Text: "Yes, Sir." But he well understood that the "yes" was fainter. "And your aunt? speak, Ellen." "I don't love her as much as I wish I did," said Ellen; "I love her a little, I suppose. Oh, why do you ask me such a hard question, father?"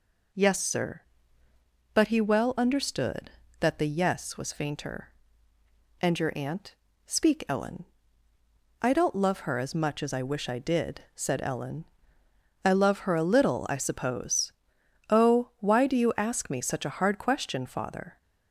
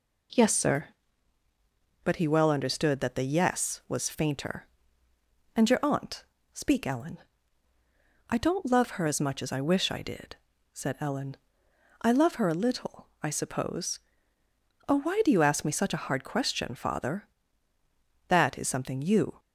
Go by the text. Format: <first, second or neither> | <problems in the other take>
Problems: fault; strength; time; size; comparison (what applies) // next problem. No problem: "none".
first | goes on to say "That is something you"; noticeable; from 18.2 s on; 1.1 s long